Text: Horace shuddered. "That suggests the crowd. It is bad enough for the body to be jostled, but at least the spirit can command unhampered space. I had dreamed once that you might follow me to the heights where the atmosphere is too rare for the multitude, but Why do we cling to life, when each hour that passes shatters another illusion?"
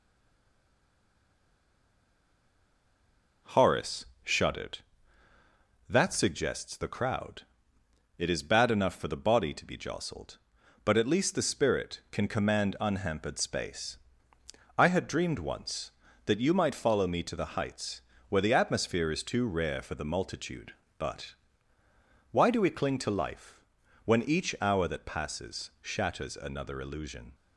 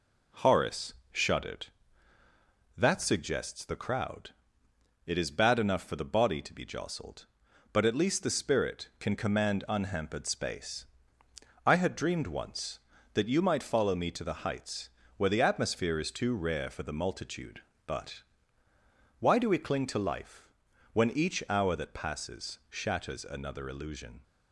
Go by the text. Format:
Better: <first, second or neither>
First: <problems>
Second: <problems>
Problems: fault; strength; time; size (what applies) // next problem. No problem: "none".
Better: second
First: stays silent before the first word; strong; until 3.4 s; 3.4 s long // pauses between "Horace" and "shuddered"; slight; at 4.0 s; 0.18 s long // pauses between "heights" and "where"; slight; at 18.0 s; 0.28 s long // pauses between "but" and "Why"; noticeable; at 21.3 s; 0.96 s long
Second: pauses between "Horace" and "shuddered"; slight; at 0.9 s; 0.18 s long // pauses between "heights" and "where"; slight; at 14.8 s; 0.28 s long // pauses between "but" and "Why"; noticeable; at 18.2 s; 0.96 s long